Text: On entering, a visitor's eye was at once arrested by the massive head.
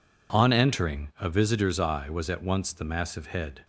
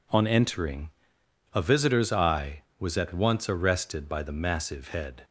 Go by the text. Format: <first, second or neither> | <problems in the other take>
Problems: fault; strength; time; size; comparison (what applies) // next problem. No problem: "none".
second | skips "arrested by"; at 2.7 s